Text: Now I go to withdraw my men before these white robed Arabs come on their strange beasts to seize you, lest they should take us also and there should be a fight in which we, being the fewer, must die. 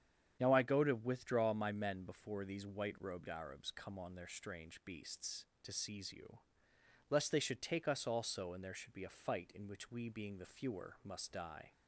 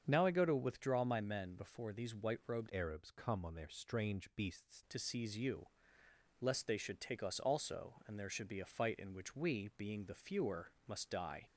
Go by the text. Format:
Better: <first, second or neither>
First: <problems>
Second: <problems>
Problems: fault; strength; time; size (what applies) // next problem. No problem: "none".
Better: first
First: starts louder than the rest; strong; until 1.4 s; 8.5 dB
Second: starts louder than the rest; strong; until 1.0 s; 7.5 dB // changes voice from "Arabs" to "beasts"; from 2.6 to 4.8 s; 2.2 s long